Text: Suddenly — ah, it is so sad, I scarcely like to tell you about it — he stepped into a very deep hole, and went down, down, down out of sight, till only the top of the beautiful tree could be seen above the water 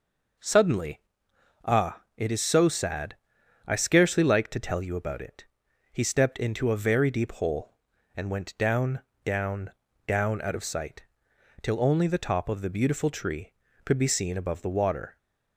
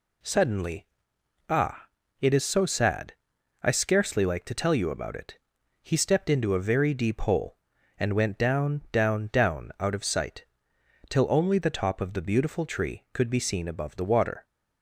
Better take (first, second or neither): neither